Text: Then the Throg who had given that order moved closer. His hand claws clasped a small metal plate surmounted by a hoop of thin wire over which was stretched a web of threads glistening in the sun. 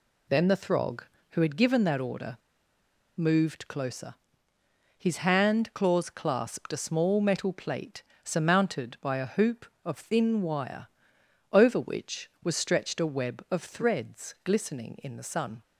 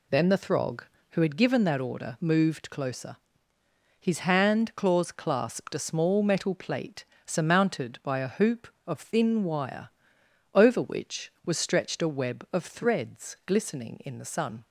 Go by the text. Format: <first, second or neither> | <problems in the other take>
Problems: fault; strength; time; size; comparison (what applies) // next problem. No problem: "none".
second | pauses between "order" and "moved"; noticeable; at 2.3 s; 0.80 s long // pauses between "plate" and "surmounted"; slight; at 8.0 s; 0.20 s long; slight in the second // pauses between "wire" and "over"; noticeable; at 10.8 s; 0.66 s long; noticeable in the second